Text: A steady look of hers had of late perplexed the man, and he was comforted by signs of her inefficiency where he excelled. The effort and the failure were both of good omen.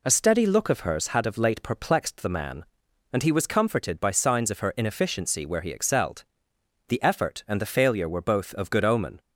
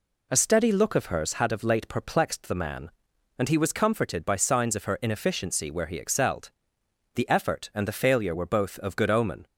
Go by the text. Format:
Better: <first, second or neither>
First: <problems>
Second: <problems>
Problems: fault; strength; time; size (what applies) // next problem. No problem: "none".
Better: neither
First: none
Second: none